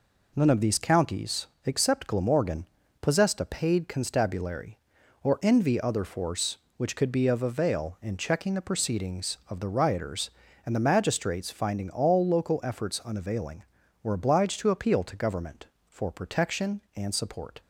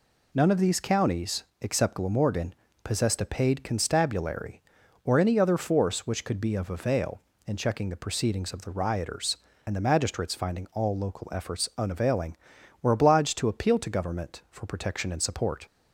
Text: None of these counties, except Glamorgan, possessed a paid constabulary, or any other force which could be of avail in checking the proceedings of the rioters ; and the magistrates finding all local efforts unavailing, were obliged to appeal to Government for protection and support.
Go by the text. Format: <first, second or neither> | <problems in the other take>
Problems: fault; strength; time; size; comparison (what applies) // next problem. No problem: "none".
second | says "envy" for "any"; at 5.4 s